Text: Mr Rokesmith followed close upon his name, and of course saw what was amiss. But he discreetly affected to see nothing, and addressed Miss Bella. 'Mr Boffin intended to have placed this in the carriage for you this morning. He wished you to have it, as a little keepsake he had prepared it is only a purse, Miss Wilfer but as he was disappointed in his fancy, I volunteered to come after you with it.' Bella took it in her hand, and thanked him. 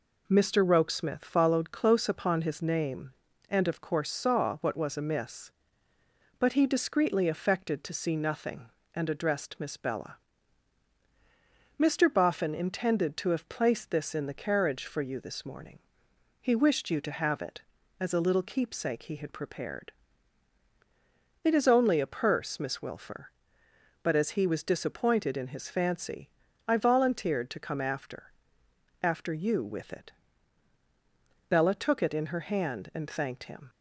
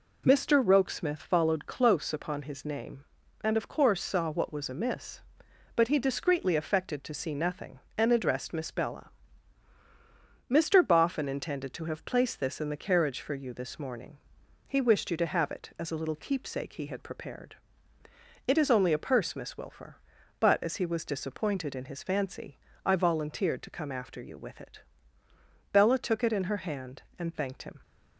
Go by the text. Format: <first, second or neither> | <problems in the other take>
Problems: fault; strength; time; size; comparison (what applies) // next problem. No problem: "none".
second | pauses between "prepared" and "it"; strong; at 19.9 s; 1.5 s long; noticeable in the second // says "after" twice; at 29.0 s